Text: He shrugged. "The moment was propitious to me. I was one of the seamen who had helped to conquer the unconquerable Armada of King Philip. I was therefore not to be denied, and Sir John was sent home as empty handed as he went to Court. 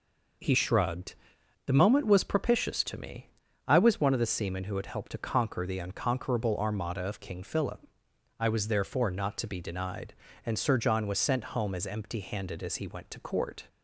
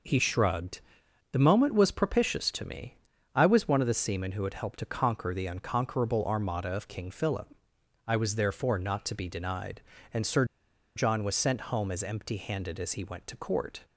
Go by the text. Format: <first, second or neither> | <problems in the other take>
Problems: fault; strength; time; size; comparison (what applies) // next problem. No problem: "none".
first | pauses between "Sir" and "John"; noticeable; at 10.4 s; 0.51 s long